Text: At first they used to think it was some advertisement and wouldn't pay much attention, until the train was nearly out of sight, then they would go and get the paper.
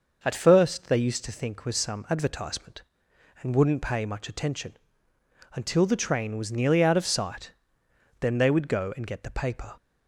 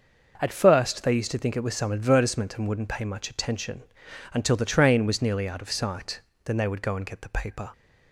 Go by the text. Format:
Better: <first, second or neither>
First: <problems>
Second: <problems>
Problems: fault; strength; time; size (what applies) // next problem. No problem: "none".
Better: second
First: skips "it"; at 1.6 s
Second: none